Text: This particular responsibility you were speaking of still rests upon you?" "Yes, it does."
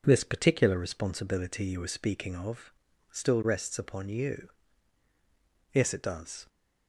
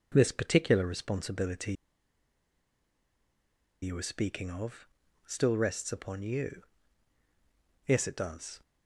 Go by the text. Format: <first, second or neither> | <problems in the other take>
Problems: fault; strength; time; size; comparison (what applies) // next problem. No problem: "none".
first | pauses between "responsibility" and "you"; strong; at 1.7 s; 2.0 s long // pauses between "of" and "still"; at 4.8 s; 0.40 s long; also in the first